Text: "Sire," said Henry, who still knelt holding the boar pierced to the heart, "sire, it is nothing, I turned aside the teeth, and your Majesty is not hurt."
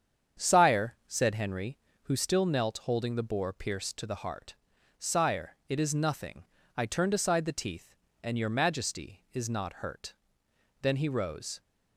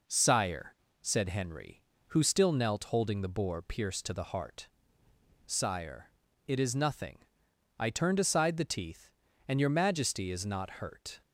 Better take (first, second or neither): second